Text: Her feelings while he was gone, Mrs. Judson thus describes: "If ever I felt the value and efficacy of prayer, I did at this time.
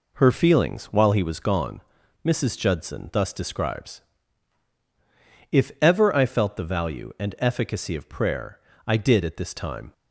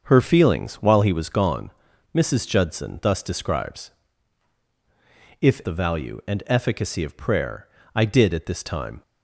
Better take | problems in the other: first | starts louder than the rest; until 1.0 s; 6.5 dB // skips "ever I felt"; at 5.6 s

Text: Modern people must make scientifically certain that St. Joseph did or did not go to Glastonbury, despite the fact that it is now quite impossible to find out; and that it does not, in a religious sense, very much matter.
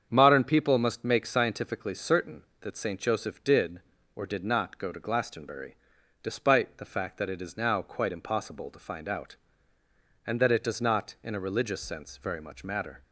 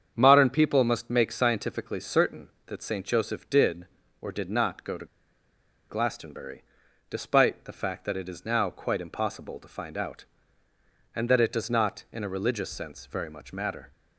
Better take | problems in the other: first | starts louder than the rest; strong; until 1.1 s; 7.5 dB; strong in the first // pauses between "to" and "Glastonbury"; noticeable; at 5.0 s; 0.83 s long

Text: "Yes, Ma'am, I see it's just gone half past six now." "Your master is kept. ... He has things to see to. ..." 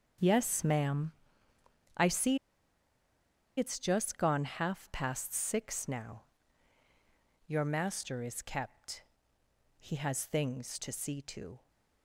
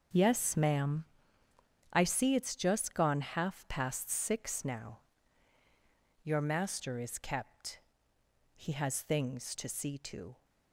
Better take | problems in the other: second | starts louder than the rest; until 2.0 s; 6.5 dB; also in the second // pauses between "see" and "it's"; at 2.3 s; 1.2 s long

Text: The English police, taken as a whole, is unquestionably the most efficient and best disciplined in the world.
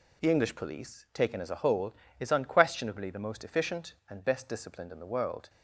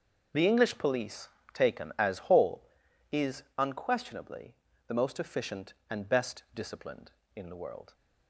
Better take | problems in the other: first | skips "a"; at 2.2 s // pauses between "unquestionably" and "the"; slight; at 4.5 s; 0.34 s long

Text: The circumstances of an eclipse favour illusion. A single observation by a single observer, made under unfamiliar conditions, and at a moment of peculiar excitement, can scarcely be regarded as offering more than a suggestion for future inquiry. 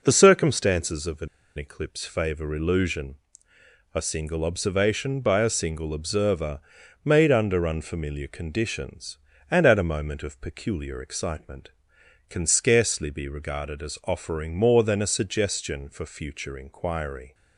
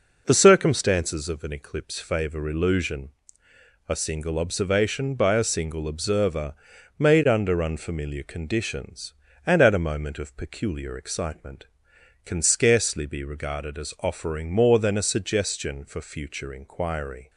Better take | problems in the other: second | pauses between "an" and "eclipse"; slight; at 1.2 s; 0.30 s long

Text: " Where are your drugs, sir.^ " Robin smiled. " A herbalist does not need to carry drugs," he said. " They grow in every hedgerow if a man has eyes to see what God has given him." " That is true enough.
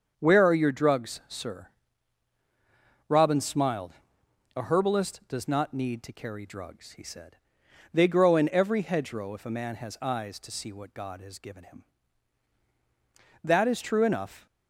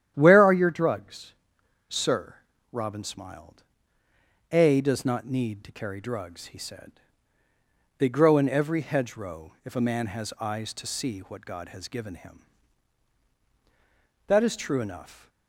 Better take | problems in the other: first | starts louder than the rest; strong; until 1.1 s; 9.5 dB; also in the first // skips "herbalist"; at 4.7 s

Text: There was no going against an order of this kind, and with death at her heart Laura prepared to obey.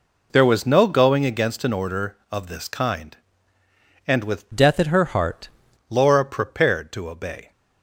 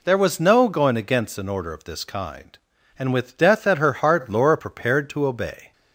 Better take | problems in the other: second | changes voice from "death" to "heart"; from 4.5 to 5.4 s; 0.9 s long

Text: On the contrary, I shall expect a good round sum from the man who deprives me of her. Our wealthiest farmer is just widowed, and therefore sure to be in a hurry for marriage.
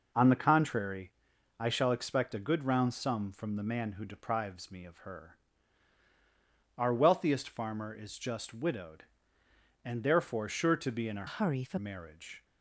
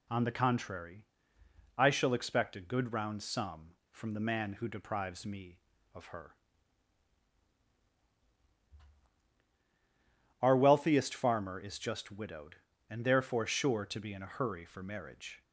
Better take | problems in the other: second | changes voice from "hurry" to "for"; from 11.2 to 11.7 s; 0.5 s long

